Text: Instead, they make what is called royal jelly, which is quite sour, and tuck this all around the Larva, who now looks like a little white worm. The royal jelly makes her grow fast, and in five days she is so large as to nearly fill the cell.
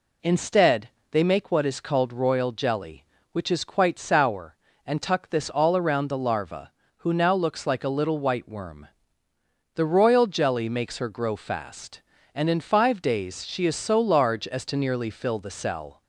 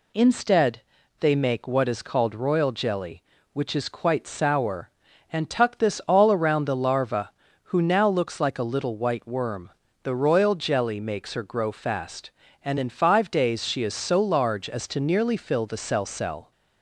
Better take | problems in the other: first | says "cell" twice; at 16.0 s

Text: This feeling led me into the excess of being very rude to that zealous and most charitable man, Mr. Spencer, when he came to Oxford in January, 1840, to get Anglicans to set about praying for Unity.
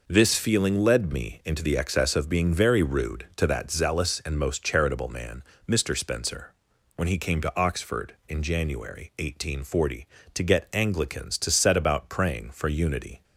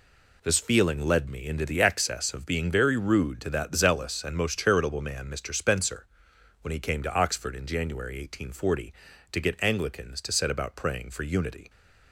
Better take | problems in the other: neither | none

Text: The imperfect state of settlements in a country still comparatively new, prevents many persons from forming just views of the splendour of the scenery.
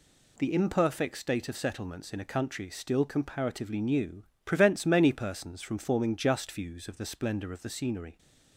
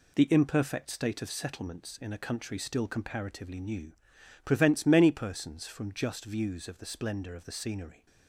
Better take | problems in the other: first | skips "forming"; at 5.9 s

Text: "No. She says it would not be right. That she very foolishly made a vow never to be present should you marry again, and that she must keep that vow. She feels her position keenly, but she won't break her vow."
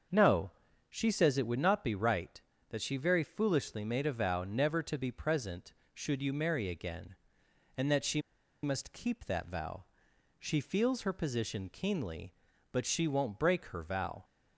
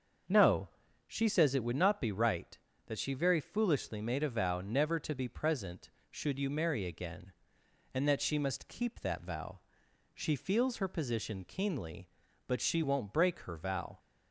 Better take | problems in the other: second | starts louder than the rest; until 1.4 s; 6.5 dB; also in the second // pauses between "she" and "must"; at 8.2 s; 0.42 s long

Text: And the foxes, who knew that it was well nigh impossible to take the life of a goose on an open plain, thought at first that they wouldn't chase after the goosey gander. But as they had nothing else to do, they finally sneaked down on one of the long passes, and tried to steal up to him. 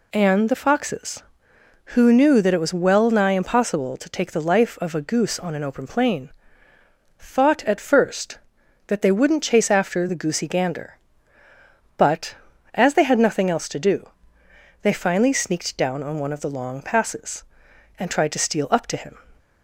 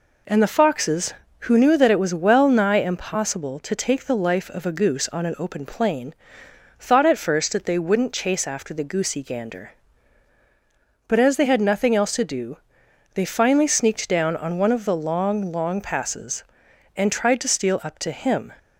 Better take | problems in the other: first | says "long" twice; at 15.5 s

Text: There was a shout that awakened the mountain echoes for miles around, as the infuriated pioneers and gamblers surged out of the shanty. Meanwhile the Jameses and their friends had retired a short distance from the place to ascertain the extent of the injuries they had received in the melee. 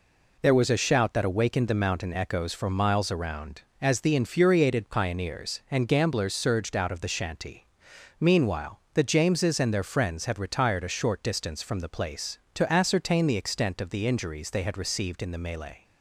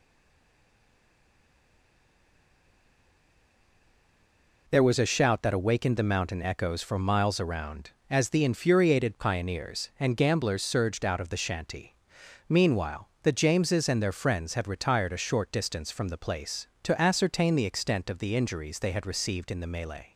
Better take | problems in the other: first | stays silent before the first word; strong; until 4.6 s; 4.6 s long

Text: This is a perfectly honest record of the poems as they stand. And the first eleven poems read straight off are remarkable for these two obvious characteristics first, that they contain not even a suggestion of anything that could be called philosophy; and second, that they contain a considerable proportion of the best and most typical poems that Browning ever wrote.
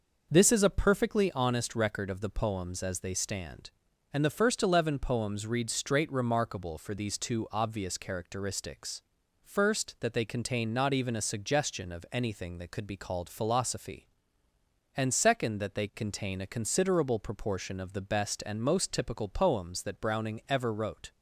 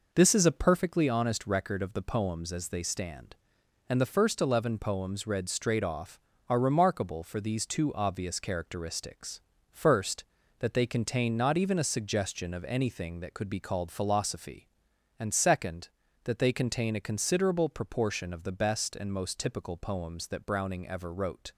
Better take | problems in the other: second | skips "off are"; at 6.1 s // pauses between "characteristics" and "first"; at 9.0 s; 0.42 s long; slight in the second

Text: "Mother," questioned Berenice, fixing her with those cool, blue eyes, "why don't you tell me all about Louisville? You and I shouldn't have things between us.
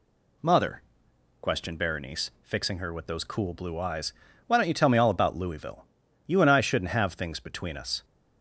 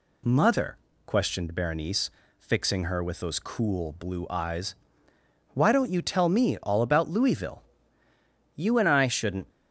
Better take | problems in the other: first | stops before "have things between us"; at 9.4 s

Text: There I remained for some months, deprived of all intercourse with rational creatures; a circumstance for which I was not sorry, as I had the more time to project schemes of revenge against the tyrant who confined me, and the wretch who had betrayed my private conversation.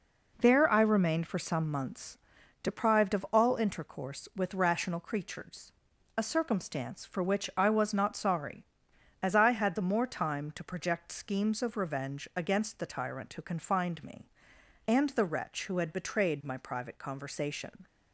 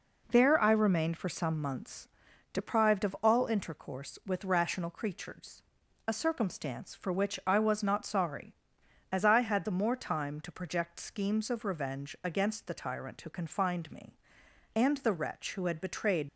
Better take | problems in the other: first | stops before "my private conversation"; at 16.2 s

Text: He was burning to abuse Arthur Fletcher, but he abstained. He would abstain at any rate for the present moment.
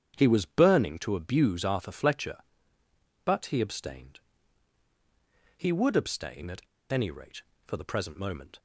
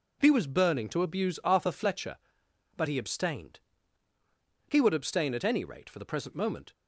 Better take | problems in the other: second | starts louder than the rest; strong; until 1.1 s; 8.5 dB // pauses between "at" and "any"; slight; at 6.6 s; 0.29 s long

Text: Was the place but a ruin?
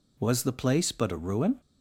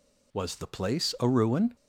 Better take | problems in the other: first | skips "but"; at 1.1 s

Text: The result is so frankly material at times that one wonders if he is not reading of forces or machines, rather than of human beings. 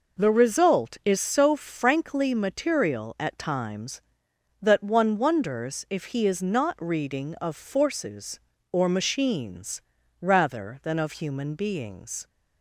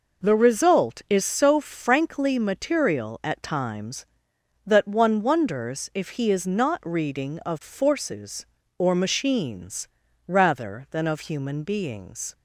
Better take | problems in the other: neither | none

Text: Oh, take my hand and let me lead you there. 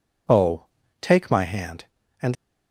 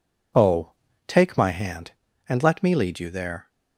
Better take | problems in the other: second | stops before "let me lead you there"; at 2.3 s

